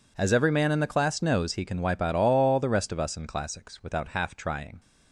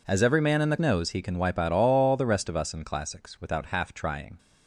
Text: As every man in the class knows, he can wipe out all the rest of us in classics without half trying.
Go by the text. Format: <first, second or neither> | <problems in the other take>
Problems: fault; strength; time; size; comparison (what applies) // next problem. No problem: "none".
first | skips "class"; at 0.7 s